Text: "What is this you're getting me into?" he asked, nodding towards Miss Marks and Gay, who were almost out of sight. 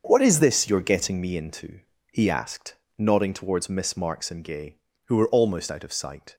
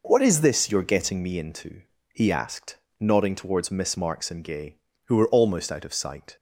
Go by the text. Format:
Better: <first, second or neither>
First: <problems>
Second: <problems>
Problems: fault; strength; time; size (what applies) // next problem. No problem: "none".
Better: second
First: gets quieter; strong; throughout; 10 dB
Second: none